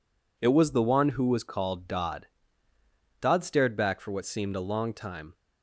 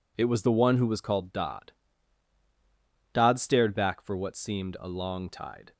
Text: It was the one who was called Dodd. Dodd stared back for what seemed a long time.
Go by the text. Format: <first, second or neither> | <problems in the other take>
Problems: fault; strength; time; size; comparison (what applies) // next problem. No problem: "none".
first | says "tide" for "time"; at 5.2 s